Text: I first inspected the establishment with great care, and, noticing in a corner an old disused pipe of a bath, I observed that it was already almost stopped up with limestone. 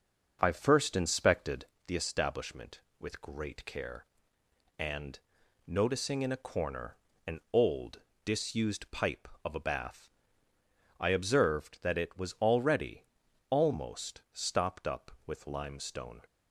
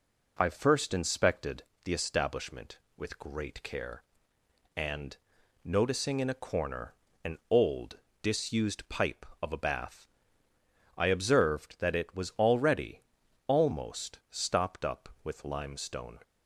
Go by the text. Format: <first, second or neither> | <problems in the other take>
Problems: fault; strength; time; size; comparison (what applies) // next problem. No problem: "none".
second | starts louder than the rest; noticeable; until 1.9 s; 6 dB // pauses between "inspected" and "the"; slight; at 1.6 s; 0.20 s long; slight in the second // pauses between "corner" and "an"; slight; at 6.9 s; 0.30 s long; slight in the second // pauses between "old" and "disused"; slight; at 7.9 s; 0.24 s long; slight in the second // pauses between "already" and "almost"; noticeable; at 13.0 s; 0.46 s long; noticeable in the second